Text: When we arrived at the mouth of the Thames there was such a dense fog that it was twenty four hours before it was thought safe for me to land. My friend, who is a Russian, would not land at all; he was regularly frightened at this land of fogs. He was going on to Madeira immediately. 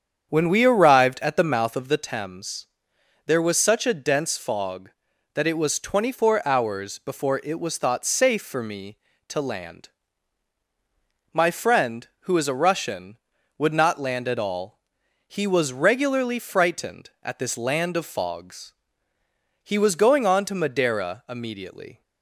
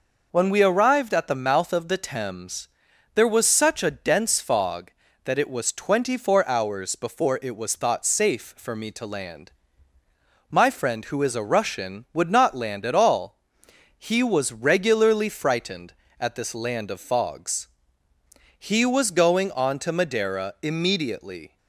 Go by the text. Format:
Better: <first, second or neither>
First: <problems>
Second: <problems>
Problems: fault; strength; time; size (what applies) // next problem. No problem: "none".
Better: second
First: starts louder than the rest; strong; until 2.1 s; 8 dB // pauses between "Thames" and "there"; noticeable; at 2.6 s; 0.60 s long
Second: pauses between "Thames" and "there"; noticeable; at 2.6 s; 0.46 s long